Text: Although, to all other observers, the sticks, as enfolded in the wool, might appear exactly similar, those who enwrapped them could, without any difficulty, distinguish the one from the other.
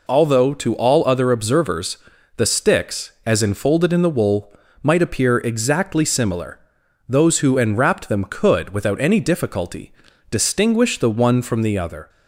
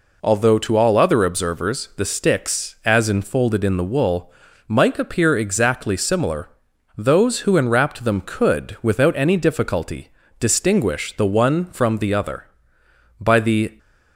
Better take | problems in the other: first | goes on to say "By the"; from 13.1 s on; 0.58 s long

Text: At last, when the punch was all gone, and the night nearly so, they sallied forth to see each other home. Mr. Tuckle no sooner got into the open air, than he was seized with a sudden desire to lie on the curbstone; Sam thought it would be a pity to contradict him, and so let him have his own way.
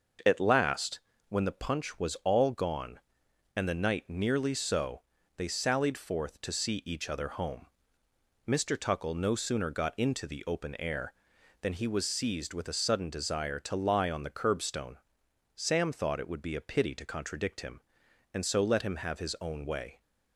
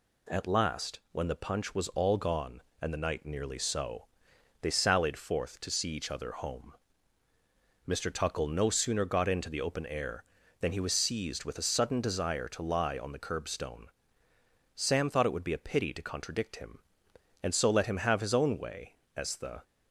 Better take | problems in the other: first | goes on to say "As the"; slight; from 19.1 s on; 0.48 s long

